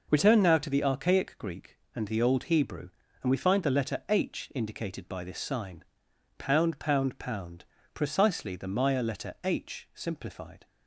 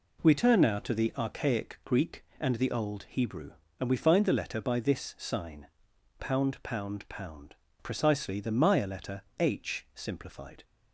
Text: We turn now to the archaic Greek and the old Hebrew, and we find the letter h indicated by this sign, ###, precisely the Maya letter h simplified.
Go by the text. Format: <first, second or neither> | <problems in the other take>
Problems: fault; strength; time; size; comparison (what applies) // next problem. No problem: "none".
first | skips "h indicated"; at 4.5 s // pauses between "letter" and "h"; slight; at 9.2 s; 0.18 s long